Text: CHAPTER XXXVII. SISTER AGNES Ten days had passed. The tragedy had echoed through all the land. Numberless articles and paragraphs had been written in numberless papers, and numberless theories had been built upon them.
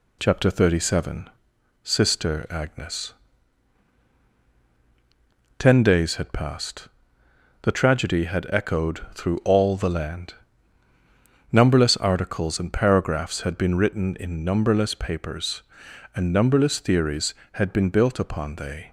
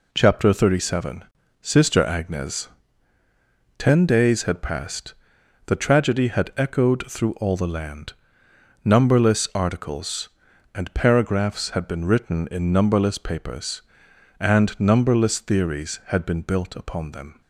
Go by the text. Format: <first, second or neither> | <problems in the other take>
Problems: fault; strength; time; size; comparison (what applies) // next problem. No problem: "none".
second | pauses between "AGNES" and "Ten"; strong; at 3.1 s; 2.4 s long; also in the second // says "they" for "them"; at 18.5 s